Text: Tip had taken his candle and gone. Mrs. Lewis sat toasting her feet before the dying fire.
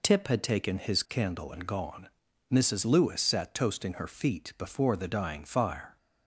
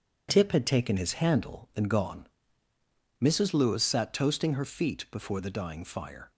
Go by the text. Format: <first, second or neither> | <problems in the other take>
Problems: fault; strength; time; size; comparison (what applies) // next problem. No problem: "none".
first | says "handle" for "candle"; at 1.1 s